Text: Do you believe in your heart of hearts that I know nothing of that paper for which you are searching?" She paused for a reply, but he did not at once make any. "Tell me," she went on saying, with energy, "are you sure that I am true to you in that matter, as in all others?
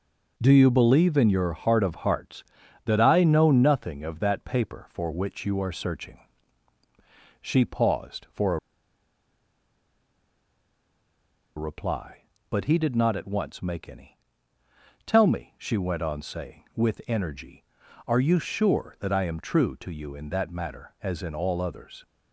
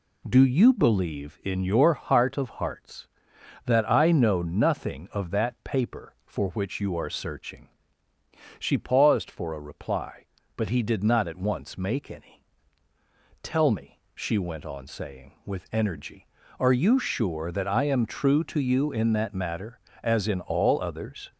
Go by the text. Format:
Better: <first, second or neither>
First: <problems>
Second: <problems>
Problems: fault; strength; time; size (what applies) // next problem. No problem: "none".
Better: second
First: pauses between "a" and "reply"; strong; at 8.5 s; 2.9 s long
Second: none